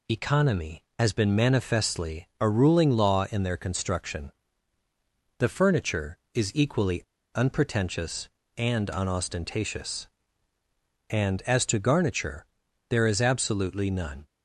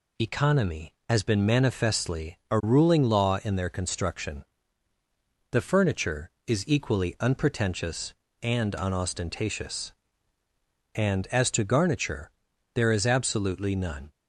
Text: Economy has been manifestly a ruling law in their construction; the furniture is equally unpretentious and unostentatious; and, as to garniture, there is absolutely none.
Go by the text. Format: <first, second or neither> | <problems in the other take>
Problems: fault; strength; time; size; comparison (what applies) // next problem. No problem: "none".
second | pauses between "equally" and "unpretentious"; slight; at 7.0 s; 0.33 s long